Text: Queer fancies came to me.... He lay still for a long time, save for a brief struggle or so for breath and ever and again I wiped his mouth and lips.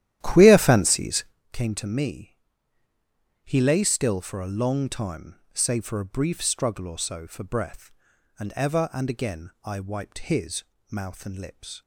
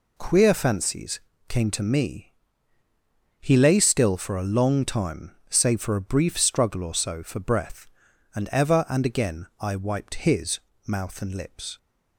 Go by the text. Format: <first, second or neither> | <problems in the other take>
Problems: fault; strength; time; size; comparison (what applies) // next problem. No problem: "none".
second | starts louder than the rest; strong; until 1.4 s; 12 dB // pauses between "fancies" and "came"; slight; at 1.2 s; 0.28 s long; slight in the second // pauses between "his" and "mouth"; slight; at 10.6 s; 0.28 s long; slight in the second